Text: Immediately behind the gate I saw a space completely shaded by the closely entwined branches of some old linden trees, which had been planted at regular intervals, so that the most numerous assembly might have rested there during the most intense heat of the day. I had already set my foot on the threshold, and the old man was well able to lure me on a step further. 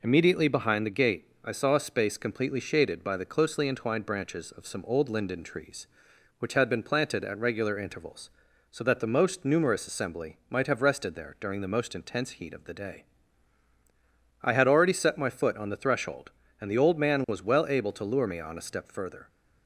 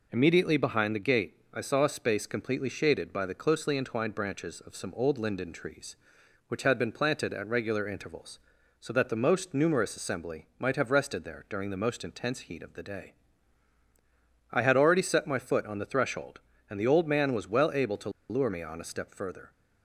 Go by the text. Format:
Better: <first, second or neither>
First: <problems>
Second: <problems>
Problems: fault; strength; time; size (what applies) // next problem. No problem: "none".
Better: first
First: pauses between "gate" and "I"; slight; at 1.2 s; 0.18 s long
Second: pauses between "gate" and "I"; slight; at 1.3 s; 0.18 s long // pauses between "to" and "lure"; slight; at 18.0 s; 0.20 s long